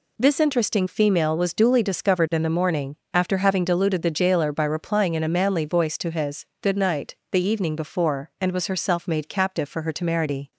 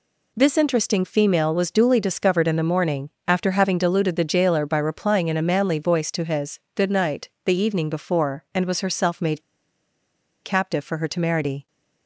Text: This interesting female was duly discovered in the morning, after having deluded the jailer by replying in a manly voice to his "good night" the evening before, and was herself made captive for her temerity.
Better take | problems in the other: first | pauses between "night" and "the"; slight; at 7.2 s; 0.16 s long; slight in the first // pauses between "made" and "captive"; at 9.4 s; 1.0 s long

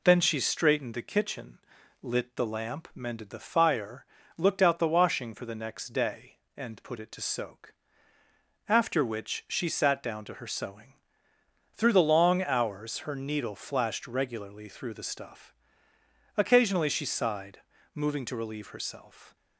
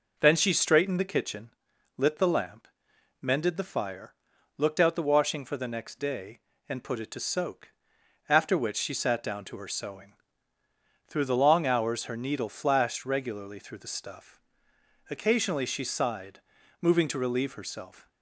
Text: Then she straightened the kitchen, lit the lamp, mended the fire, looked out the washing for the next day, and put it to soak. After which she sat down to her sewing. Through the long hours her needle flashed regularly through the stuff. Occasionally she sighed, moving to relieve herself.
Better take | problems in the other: neither | none

